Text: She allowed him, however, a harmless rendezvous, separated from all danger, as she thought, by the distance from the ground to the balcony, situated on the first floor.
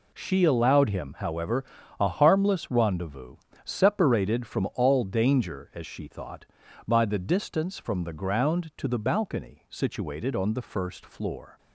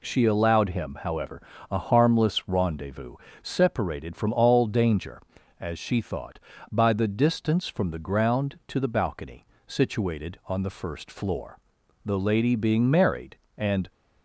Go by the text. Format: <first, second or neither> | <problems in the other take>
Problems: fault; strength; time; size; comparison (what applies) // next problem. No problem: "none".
first | goes on to say "The lady being married and"; strong; from 12.0 s on; 1.8 s long